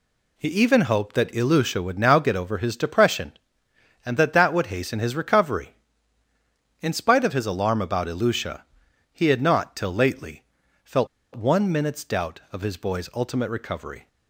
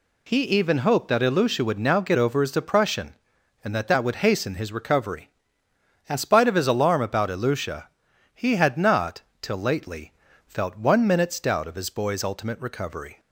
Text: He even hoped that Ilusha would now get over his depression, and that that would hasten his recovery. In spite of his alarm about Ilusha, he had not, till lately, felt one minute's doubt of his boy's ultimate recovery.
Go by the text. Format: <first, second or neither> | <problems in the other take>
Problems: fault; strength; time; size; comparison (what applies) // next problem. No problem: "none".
second | pauses between "felt" and "one"; slight; at 11.0 s; 0.28 s long